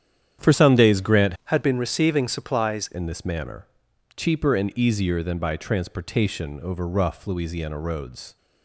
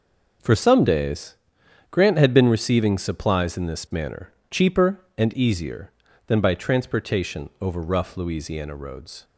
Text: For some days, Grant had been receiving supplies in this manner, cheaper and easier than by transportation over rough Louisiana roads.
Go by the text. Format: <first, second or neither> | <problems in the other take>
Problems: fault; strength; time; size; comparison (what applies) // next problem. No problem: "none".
second | starts louder than the rest; strong; until 1.5 s; 9.5 dB // changes voice from "had" to "supplies"; from 1.4 to 2.8 s; 1.4 s long